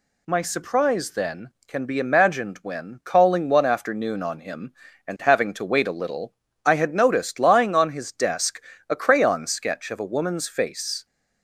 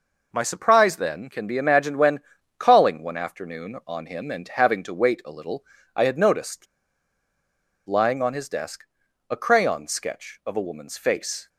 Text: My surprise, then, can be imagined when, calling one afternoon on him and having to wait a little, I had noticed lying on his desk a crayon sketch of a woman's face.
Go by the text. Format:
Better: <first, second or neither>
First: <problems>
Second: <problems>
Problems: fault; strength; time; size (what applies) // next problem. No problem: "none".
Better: first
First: pauses between "desk" and "a"; slight; at 8.6 s; 0.28 s long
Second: pauses between "noticed" and "lying"; at 6.6 s; 1.2 s long // pauses between "desk" and "a"; at 8.8 s; 0.44 s long